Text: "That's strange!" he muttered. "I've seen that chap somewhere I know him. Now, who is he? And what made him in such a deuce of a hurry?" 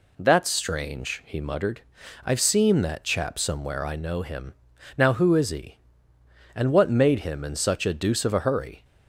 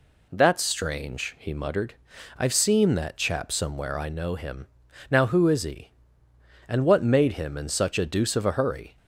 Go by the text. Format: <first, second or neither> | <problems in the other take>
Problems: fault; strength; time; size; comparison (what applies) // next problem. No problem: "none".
neither | none